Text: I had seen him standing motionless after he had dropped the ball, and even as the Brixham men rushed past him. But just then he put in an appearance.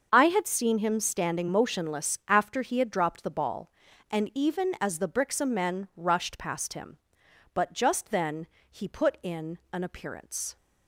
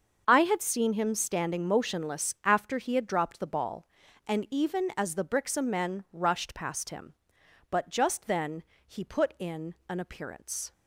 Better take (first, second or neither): neither